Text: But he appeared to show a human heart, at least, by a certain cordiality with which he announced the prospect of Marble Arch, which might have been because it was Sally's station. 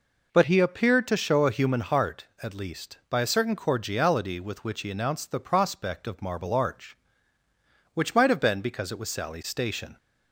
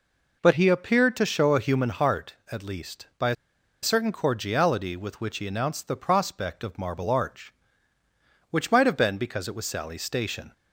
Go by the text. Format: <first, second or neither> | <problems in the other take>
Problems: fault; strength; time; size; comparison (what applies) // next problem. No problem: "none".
first | pauses between "a" and "certain"; noticeable; at 3.3 s; 0.47 s long